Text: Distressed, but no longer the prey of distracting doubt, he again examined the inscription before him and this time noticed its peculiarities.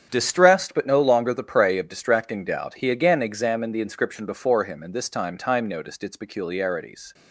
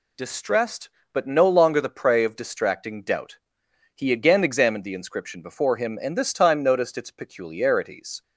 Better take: second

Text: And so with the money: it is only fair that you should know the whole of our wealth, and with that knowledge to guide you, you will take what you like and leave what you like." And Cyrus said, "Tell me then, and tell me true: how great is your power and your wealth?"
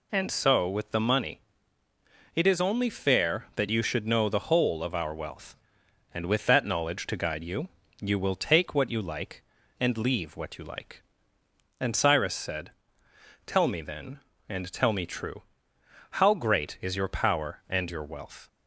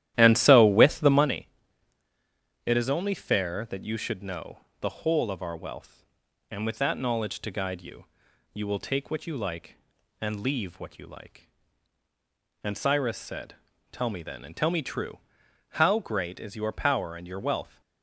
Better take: first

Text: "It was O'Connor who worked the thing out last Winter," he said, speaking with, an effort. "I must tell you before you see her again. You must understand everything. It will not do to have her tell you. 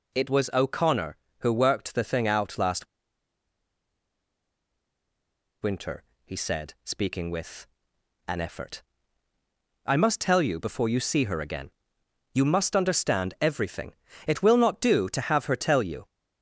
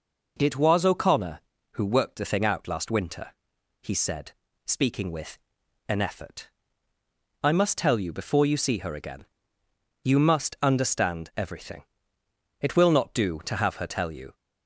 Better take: second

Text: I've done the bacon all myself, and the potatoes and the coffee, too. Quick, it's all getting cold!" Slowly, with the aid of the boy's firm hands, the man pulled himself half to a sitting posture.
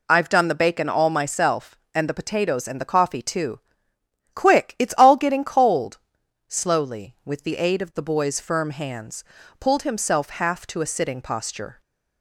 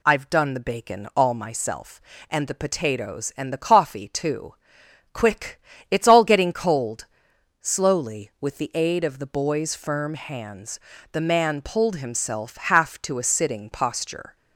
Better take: second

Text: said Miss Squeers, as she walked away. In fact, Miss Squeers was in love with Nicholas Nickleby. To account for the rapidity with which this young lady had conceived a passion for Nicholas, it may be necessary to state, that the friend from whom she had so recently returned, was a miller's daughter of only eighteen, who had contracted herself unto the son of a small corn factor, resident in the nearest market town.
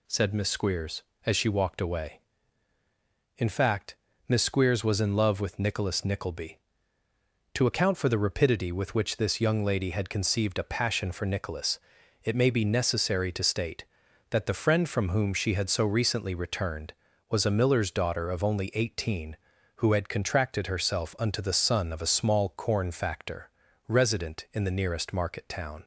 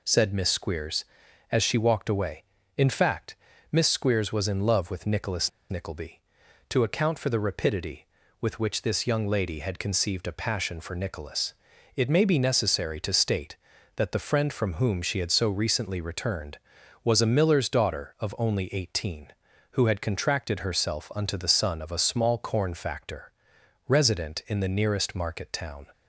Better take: first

